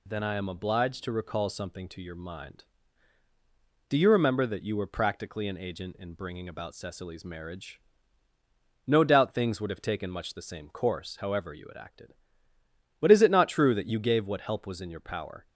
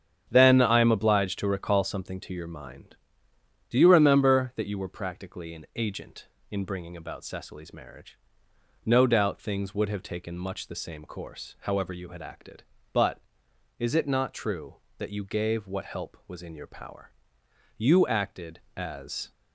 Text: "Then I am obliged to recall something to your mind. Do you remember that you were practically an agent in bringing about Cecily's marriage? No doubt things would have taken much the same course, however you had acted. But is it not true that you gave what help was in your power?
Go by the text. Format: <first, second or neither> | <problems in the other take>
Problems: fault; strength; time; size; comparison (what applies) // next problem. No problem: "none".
first | starts louder than the rest; strong; until 1.2 s; 8 dB // goes on to say "You acted as"; from 17.7 s on; 1.5 s long